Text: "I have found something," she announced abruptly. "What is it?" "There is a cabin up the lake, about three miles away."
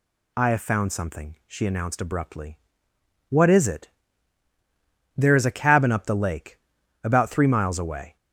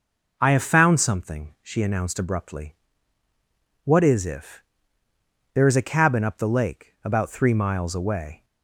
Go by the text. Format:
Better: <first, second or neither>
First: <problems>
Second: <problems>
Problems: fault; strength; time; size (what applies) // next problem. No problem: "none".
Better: first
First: none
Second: says "if" for "it"; at 4.2 s